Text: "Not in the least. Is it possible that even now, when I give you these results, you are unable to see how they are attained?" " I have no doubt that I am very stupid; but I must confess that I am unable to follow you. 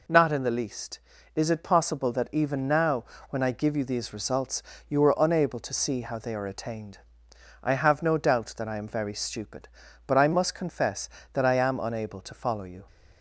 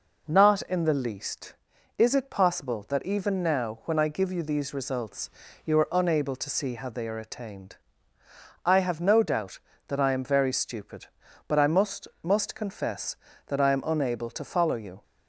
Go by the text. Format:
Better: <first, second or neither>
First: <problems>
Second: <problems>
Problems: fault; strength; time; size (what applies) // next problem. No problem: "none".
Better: first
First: none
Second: says "must" twice; at 12.2 s